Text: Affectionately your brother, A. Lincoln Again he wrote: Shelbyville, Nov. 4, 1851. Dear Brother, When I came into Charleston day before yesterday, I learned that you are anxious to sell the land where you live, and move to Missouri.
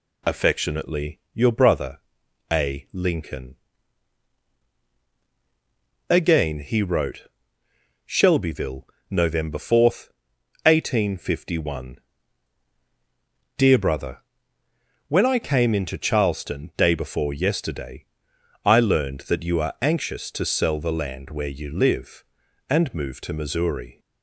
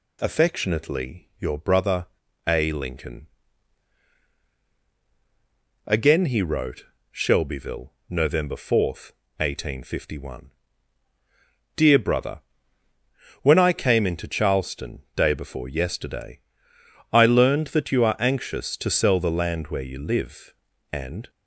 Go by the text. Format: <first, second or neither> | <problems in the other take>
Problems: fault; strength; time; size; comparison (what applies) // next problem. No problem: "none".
first | pauses between "Lincoln" and "Again"; strong; at 3.2 s; 2.6 s long; strong in the first // stops before "move to Missouri"; at 21.2 s